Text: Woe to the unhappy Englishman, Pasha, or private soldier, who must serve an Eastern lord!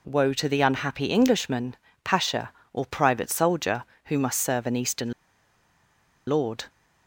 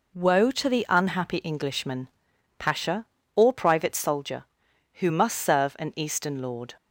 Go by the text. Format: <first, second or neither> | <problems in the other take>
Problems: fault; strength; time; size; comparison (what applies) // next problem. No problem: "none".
second | pauses between "Eastern" and "lord"; at 5.1 s; 1.1 s long